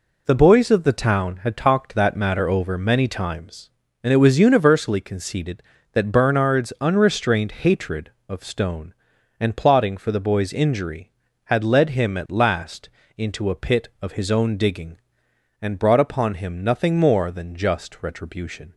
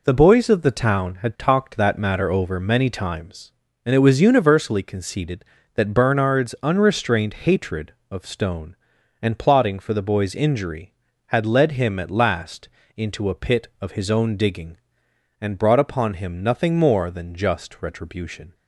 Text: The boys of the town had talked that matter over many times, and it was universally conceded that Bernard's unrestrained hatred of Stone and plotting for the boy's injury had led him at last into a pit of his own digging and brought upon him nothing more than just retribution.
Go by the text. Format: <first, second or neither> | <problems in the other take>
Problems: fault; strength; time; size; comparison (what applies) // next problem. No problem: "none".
neither | pauses between "last" and "into"; slight; the same in both